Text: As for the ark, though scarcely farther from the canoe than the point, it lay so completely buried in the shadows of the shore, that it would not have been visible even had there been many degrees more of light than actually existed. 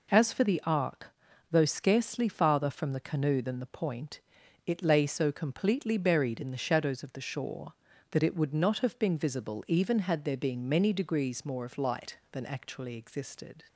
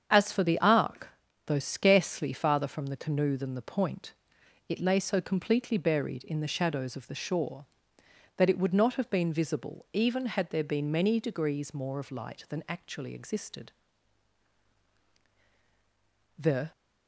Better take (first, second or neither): first